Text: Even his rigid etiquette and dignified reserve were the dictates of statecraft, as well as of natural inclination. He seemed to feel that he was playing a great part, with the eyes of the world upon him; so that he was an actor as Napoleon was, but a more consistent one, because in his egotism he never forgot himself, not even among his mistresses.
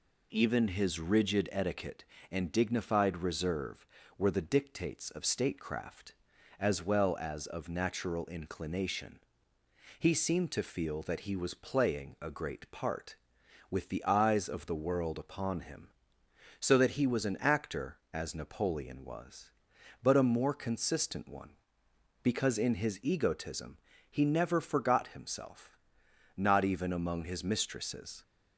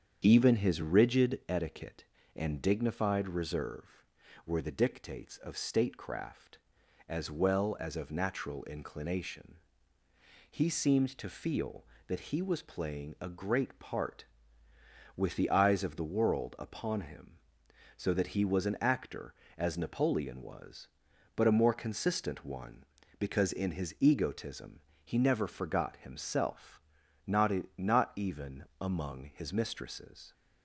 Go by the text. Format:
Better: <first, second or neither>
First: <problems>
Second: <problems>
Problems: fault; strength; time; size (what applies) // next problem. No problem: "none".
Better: first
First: pauses between "egotism" and "he"; slight; at 23.7 s; 0.30 s long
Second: starts louder than the rest; strong; until 1.2 s; 7.5 dB // pauses between "egotism" and "he"; slight; at 24.7 s; 0.24 s long // says "not" twice; at 27.7 s // pauses between "even" and "among"; slight; at 28.6 s; 0.16 s long